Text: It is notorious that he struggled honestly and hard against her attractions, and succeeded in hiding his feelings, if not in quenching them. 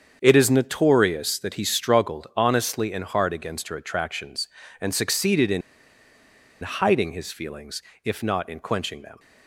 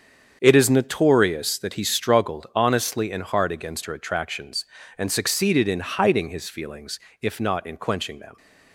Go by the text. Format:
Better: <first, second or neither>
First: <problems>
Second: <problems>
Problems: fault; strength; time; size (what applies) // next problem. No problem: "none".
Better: second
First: starts louder than the rest; strong; until 1.2 s; 7 dB // pauses between "in" and "hiding"; at 5.6 s; 1.0 s long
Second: starts louder than the rest; strong; until 1.4 s; 7 dB